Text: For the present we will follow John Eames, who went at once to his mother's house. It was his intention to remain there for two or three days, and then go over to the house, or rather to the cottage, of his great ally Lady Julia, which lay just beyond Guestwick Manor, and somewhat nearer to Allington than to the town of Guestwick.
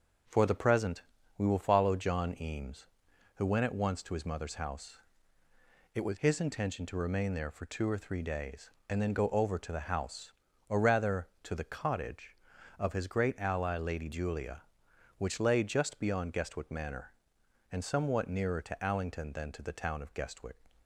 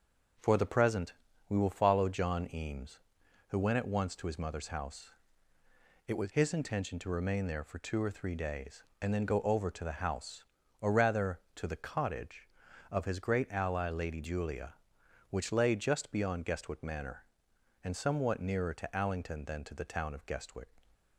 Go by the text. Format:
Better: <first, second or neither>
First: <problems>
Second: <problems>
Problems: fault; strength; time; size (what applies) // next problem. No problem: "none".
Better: neither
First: starts louder than the rest; until 1.6 s; 6 dB // pauses between "present" and "we"; at 1.0 s; 0.38 s long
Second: starts louder than the rest; until 1.7 s; 6.5 dB // pauses between "present" and "we"; at 1.1 s; 0.38 s long